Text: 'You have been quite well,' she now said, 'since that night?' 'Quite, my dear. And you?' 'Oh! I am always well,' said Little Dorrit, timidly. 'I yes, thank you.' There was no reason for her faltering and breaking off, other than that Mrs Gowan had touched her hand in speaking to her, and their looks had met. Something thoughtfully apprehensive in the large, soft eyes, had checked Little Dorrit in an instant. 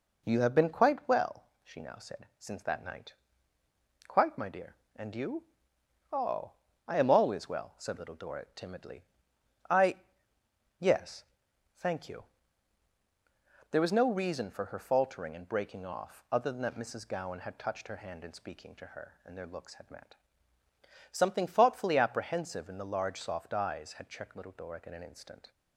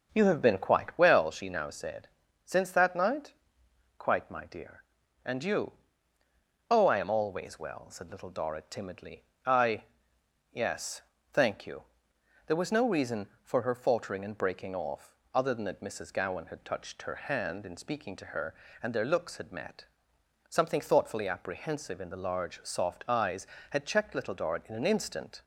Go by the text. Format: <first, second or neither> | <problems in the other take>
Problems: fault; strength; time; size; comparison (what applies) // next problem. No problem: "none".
first | starts louder than the rest; noticeable; until 1.0 s; 6 dB // pauses between "I" and "yes"; noticeable; at 9.8 s; 0.68 s long; noticeable in the first